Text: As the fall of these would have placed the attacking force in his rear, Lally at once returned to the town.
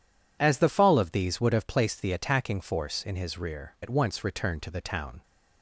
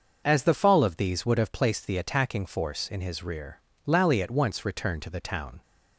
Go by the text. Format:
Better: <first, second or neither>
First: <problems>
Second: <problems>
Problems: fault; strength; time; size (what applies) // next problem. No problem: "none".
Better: second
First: skips "Lally"; at 3.7 s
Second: none